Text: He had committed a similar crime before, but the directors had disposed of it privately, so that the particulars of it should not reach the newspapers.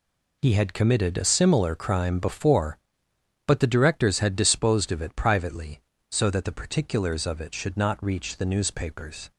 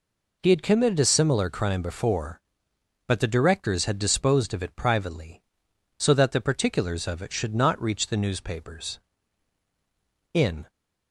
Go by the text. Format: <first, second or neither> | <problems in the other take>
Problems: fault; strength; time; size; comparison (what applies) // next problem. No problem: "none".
first | goes on to say "In"; slight; from 10.3 s on; 0.38 s long